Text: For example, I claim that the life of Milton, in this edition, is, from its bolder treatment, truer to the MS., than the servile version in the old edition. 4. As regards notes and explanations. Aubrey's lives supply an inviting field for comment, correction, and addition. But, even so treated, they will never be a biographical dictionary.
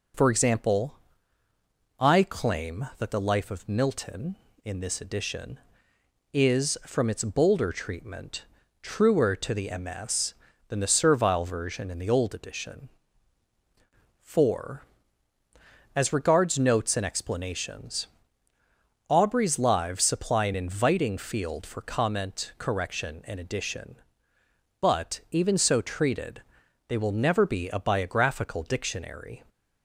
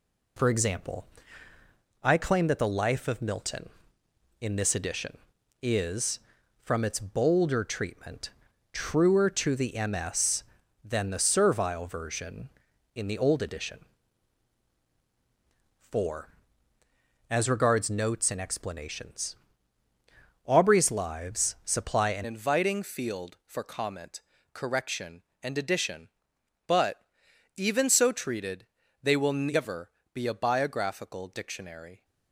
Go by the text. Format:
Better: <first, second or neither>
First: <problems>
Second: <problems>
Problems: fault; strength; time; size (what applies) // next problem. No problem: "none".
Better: first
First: none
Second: changes voice at "inviting"; from 22.2 s on; 9.8 s long // pauses between "never" and "be"; slight; at 29.9 s; 0.24 s long